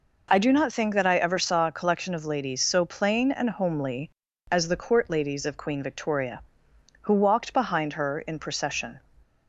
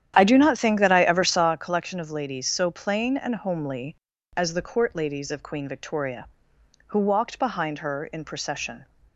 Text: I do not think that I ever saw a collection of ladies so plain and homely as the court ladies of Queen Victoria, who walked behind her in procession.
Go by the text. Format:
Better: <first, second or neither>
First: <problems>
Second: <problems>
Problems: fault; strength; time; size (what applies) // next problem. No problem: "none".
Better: first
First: none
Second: starts louder than the rest; strong; until 1.7 s; 10 dB